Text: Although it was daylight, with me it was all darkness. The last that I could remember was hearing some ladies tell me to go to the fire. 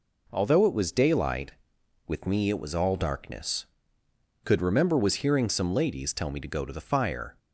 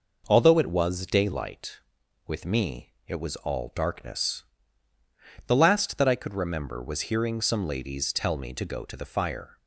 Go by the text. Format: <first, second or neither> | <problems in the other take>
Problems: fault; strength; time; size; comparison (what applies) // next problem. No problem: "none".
second | skips "The last that I"; at 4.0 s